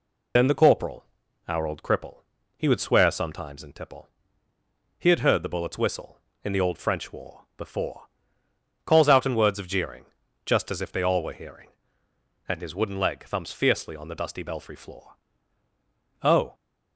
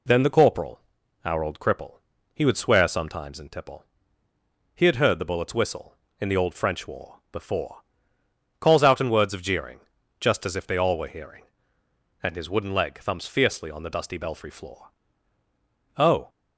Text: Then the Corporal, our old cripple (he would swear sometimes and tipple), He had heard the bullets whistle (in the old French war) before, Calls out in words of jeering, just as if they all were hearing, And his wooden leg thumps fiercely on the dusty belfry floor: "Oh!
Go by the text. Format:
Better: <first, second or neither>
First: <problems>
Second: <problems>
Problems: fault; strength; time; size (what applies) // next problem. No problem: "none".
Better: second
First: loses the start of "Then"; at 0.3 s; 45 ms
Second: none